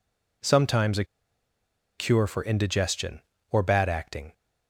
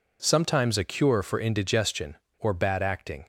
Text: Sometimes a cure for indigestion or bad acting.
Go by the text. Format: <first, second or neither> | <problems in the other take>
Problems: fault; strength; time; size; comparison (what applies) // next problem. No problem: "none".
second | pauses between "a" and "cure"; noticeable; at 1.0 s; 0.94 s long